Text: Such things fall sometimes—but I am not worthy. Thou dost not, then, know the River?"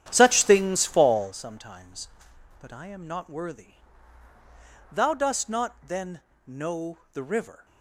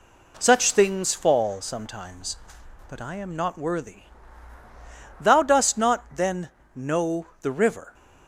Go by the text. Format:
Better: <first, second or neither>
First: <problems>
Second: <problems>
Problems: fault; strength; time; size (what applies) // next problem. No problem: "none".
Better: second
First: starts louder than the rest; strong; until 1.4 s; 9.5 dB // pauses between "know" and "the"; slight; at 6.9 s; 0.16 s long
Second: pauses between "know" and "the"; slight; at 7.2 s; 0.16 s long